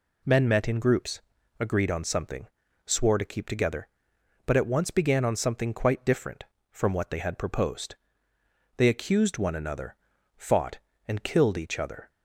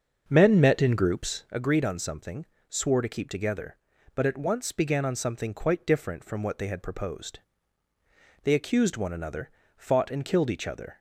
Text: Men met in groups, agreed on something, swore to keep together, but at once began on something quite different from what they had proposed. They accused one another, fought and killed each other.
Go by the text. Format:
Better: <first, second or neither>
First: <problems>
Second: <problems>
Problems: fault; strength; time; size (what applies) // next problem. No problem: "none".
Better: first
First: none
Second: starts louder than the rest; until 1.5 s; 7 dB